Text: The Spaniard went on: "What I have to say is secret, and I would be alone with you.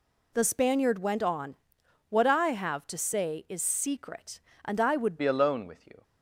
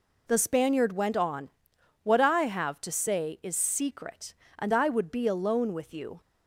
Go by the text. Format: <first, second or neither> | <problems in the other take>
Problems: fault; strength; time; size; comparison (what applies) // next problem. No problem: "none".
second | changes voice at "be"; from 5.1 s on; 0.9 s long